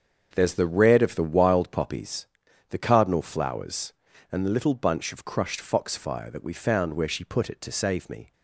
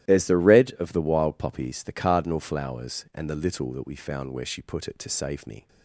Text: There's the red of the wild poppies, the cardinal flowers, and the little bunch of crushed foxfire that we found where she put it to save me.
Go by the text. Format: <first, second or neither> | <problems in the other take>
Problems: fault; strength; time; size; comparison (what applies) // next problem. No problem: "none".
first | starts louder than the rest; strong; until 1.1 s; 14 dB; also in the first // skips "bunch of crushed foxfire"; at 3.7 s